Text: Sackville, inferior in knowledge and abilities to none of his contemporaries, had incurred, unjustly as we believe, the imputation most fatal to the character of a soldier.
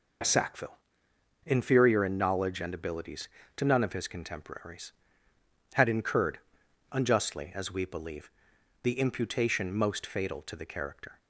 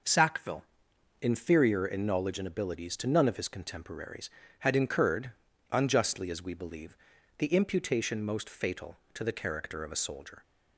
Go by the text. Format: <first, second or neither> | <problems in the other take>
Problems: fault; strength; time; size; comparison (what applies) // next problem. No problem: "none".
second | stops before "of a soldier"; at 11.1 s